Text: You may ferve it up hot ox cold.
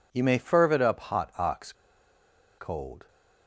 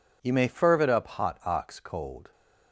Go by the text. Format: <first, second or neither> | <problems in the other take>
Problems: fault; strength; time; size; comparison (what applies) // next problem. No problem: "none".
second | pauses between "ox" and "cold"; noticeable; at 1.7 s; 0.86 s long